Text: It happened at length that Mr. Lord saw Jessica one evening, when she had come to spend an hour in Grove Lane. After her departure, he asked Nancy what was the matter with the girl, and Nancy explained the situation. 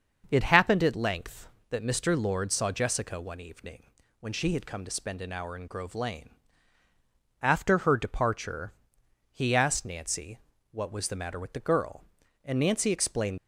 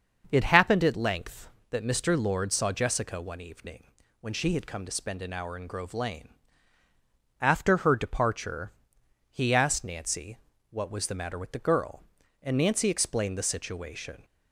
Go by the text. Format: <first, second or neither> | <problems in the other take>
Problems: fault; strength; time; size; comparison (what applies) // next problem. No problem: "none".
second | starts louder than the rest; until 1.3 s; 6.5 dB; also in the second // pauses between "Nancy" and "what"; slight; at 10.3 s; 0.34 s long; slight in the second // stops before "the situation"; at 13.3 s